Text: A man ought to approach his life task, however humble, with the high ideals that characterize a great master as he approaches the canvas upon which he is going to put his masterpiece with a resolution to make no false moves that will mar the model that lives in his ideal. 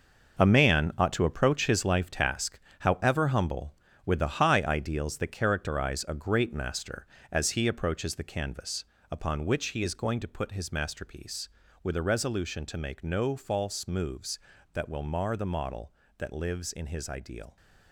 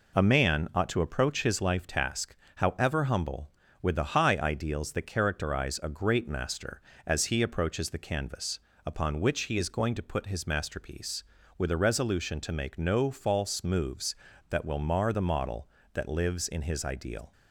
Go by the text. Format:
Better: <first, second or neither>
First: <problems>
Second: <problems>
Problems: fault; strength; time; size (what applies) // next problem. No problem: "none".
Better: second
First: gets quieter; strong; throughout; 10 dB // pauses between "canvas" and "upon"; slight; at 8.8 s; 0.26 s long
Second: pauses between "canvas" and "upon"; slight; at 8.5 s; 0.26 s long